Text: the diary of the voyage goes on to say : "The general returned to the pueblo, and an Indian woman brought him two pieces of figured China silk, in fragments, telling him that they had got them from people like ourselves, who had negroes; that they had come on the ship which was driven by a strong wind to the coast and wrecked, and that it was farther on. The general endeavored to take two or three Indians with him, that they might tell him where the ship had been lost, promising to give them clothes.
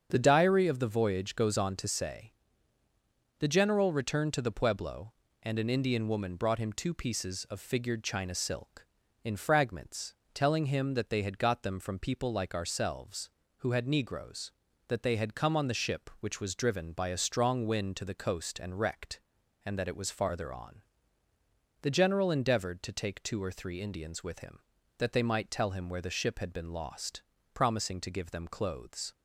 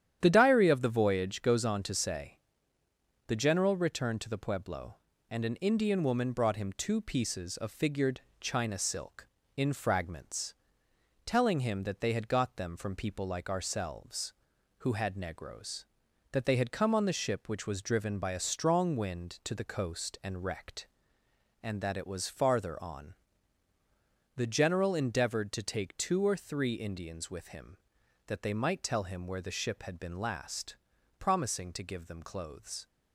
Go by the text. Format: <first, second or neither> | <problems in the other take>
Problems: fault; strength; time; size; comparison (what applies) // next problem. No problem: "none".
first | starts louder than the rest; strong; until 1.2 s; 10 dB; strong in the first // pauses between "figured" and "China"; slight; at 8.2 s; 0.18 s long // says "last" for "lost"; at 30.1 s